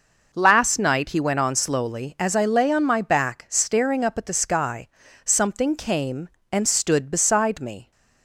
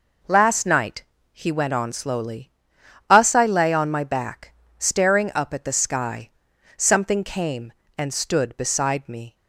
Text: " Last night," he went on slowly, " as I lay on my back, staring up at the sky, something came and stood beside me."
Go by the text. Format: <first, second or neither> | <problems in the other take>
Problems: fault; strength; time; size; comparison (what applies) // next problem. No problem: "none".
first | says "us" for "as"; at 3.1 s